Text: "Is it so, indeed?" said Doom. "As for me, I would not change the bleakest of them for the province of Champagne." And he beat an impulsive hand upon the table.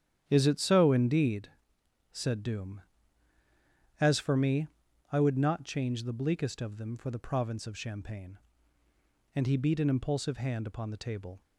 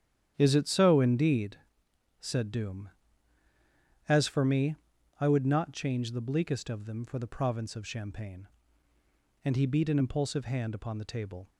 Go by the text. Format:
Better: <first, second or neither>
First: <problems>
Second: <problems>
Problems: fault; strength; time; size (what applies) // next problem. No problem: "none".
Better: neither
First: starts louder than the rest; strong; until 1.2 s; 10.5 dB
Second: starts louder than the rest; strong; until 1.3 s; 10.5 dB